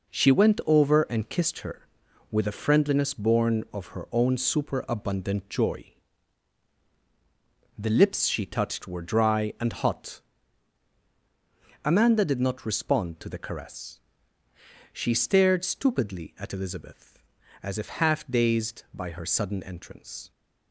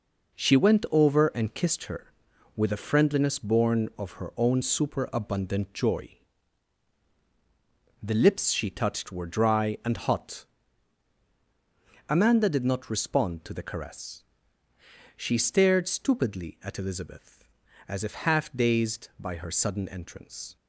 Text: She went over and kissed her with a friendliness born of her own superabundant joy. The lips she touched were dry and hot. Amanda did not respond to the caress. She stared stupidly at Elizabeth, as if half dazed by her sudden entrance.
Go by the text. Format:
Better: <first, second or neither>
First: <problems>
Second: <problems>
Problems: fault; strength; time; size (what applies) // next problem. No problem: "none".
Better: neither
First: none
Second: none